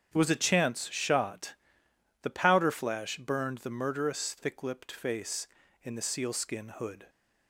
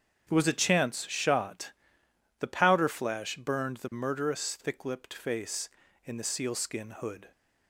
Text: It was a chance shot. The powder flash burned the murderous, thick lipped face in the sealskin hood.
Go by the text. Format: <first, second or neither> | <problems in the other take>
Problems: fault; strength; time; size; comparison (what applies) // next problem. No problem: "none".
neither | starts louder than the rest; strong; the same in both